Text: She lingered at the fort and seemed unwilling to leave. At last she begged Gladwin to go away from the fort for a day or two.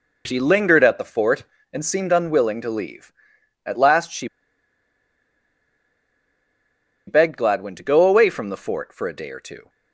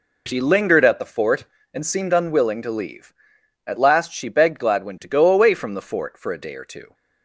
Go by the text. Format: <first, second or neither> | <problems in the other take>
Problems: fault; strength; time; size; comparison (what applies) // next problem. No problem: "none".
second | pauses between "she" and "begged"; strong; at 4.2 s; 2.8 s long